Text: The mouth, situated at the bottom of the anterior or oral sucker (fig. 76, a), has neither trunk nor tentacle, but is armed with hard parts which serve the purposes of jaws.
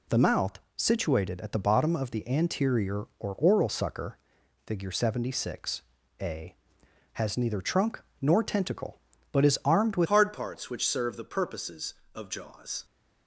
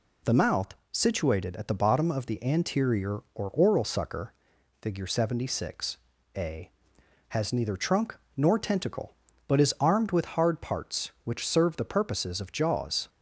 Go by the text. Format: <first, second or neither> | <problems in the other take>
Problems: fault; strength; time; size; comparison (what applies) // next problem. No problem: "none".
second | pauses between "trunk" and "nor"; slight; at 8.0 s; 0.18 s long; slight in the second // changes voice at "hard"; from 10.0 s on; 2.8 s long